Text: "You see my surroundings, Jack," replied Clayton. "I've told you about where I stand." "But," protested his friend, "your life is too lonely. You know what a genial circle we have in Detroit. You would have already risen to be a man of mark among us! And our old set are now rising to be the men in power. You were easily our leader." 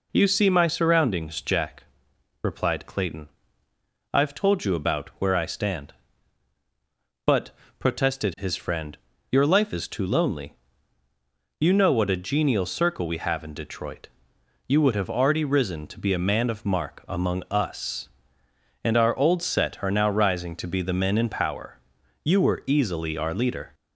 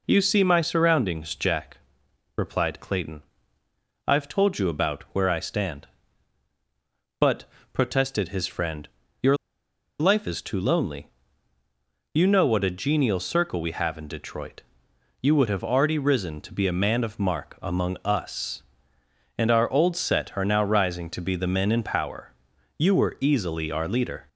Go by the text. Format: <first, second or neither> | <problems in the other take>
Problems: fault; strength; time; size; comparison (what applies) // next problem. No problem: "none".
first | pauses between "your" and "life"; noticeable; at 9.3 s; 0.64 s long